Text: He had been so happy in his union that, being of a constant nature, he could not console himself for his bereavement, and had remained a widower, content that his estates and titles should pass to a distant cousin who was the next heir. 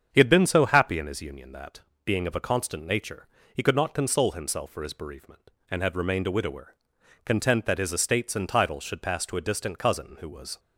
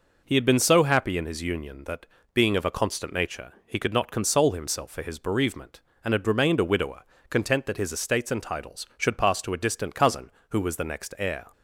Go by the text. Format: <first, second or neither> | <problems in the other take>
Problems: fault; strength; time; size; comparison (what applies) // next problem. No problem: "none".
second | starts louder than the rest; strong; until 1.1 s; 7.5 dB // stops before "the next heir"; at 10.5 s